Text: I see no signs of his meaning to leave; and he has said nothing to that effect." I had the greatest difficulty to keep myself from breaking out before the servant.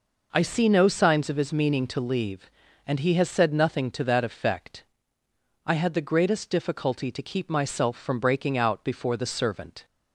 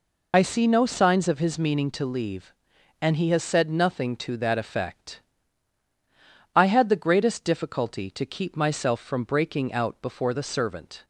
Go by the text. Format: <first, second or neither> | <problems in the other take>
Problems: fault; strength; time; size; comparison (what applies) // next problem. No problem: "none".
first | loses the start of "I"; at 0.3 s; 50 ms